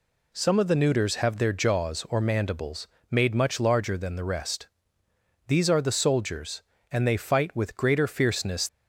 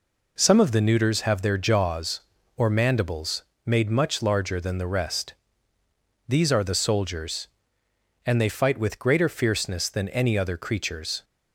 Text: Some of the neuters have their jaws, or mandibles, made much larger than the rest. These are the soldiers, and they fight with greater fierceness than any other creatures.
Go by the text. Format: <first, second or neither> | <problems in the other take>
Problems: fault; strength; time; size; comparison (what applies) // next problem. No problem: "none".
second | stops before "than any other creatures"; at 8.6 s